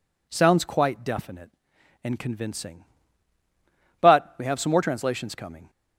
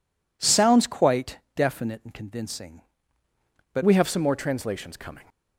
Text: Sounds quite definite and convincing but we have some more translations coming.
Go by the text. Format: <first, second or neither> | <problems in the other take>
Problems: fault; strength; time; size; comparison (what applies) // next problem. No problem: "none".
first | pauses between "quite" and "definite"; slight; at 1.3 s; 0.16 s long // changes voice at "we"; from 3.8 s on; 1.4 s long